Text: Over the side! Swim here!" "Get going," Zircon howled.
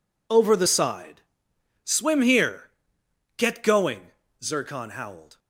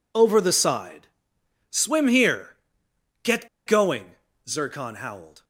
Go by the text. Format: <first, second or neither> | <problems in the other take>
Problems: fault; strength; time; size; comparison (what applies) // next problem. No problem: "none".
first | pauses between "Get" and "going"; slight; at 3.4 s; 0.18 s long